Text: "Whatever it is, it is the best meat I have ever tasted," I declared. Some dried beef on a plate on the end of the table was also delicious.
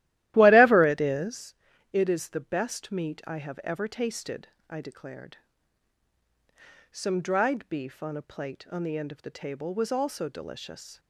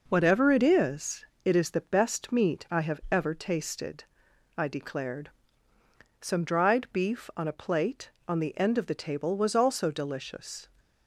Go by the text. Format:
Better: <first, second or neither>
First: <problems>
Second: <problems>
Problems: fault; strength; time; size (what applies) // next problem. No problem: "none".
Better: second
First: starts louder than the rest; strong; until 1.4 s; 14.5 dB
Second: none